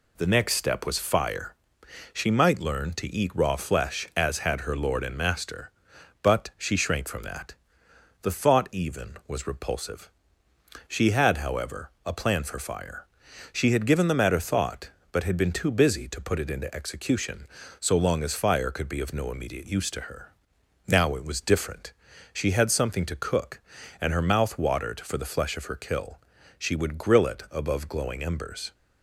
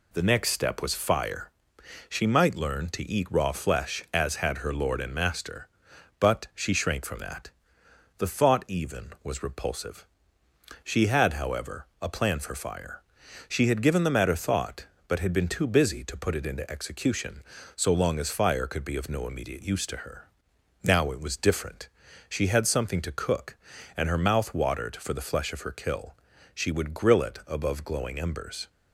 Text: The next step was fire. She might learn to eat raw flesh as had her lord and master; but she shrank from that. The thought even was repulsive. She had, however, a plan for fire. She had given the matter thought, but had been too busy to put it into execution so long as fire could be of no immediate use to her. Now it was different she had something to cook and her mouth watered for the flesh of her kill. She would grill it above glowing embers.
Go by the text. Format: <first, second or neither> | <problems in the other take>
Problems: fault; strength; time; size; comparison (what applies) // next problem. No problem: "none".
neither | pauses between "different" and "she"; the same in both